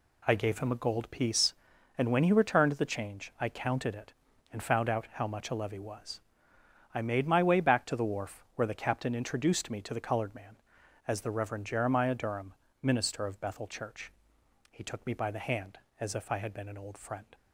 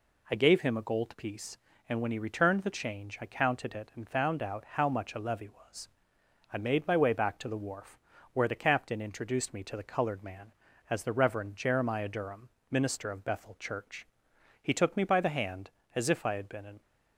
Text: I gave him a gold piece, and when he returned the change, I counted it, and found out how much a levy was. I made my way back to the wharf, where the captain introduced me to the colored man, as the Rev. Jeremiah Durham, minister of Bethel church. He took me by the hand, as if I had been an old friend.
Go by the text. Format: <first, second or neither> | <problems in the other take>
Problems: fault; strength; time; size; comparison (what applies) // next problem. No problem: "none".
first | stops before "old friend"; at 16.8 s